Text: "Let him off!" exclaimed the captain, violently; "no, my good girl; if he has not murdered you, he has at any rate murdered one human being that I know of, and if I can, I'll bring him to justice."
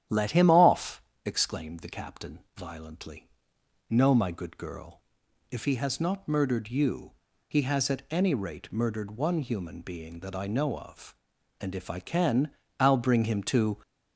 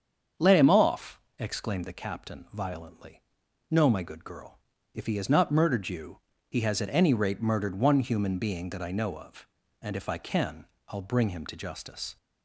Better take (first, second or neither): second